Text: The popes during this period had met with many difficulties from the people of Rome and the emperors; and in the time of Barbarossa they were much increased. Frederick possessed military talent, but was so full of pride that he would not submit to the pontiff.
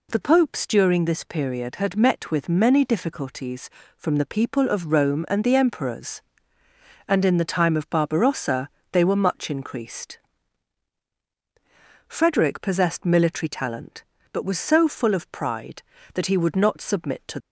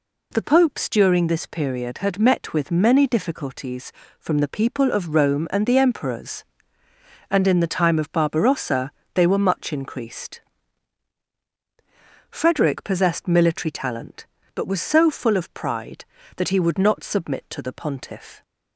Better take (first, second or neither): second